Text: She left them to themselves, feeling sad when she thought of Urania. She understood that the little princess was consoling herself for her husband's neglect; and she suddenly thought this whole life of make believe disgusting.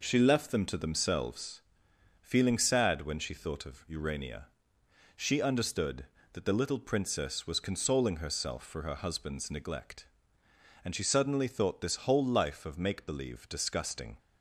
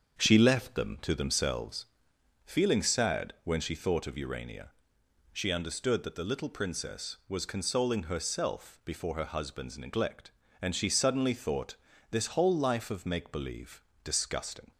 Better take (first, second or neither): first